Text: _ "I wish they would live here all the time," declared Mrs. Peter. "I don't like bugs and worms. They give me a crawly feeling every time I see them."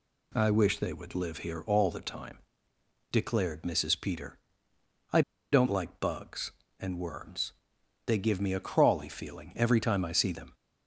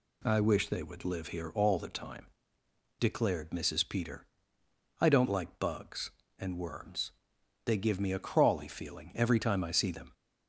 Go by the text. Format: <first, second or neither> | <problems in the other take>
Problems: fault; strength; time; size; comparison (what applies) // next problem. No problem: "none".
second | pauses between "I" and "don't"; slight; at 5.2 s; 0.31 s long